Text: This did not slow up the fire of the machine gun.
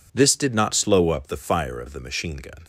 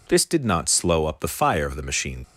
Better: first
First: none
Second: stops before "gun"; at 2.2 s

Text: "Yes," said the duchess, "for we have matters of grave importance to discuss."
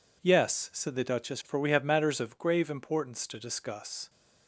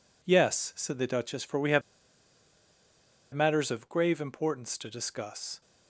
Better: first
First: none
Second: pauses between "have" and "matters"; strong; at 1.8 s; 1.5 s long

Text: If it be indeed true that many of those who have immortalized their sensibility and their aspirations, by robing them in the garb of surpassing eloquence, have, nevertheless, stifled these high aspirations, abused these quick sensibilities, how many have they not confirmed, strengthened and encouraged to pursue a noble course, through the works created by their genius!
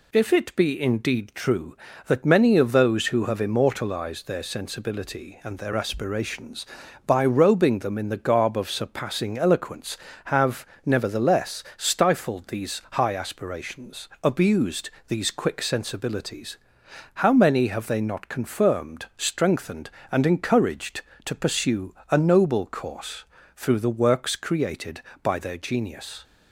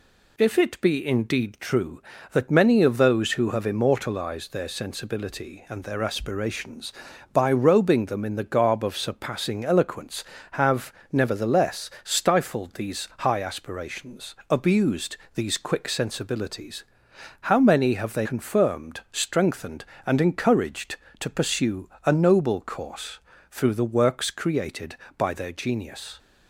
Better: first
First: pauses between "abused" and "these"; slight; at 14.9 s; 0.16 s long // pauses between "pursue" and "a"; slight; at 21.9 s; 0.16 s long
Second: pauses between "abused" and "these"; slight; at 15.1 s; 0.16 s long // skips "not"; at 18.2 s // pauses between "pursue" and "a"; slight; at 21.8 s; 0.16 s long

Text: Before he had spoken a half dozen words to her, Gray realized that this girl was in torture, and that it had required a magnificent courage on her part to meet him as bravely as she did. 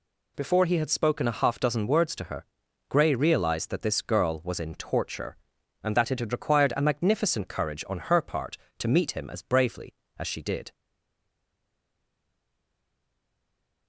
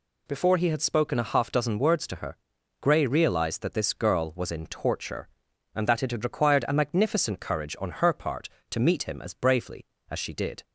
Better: second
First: stays silent after the last word; strong; from 10.7 s on; 3.1 s long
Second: none

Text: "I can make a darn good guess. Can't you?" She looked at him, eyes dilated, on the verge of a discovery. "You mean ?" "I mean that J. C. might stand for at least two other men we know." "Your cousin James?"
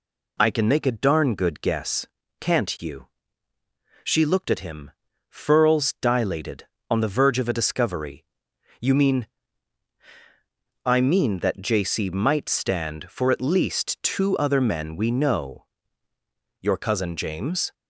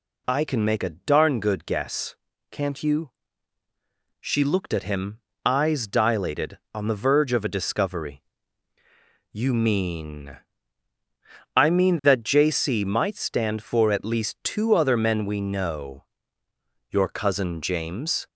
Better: second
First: says "furls" for "eyes"; at 5.2 s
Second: none

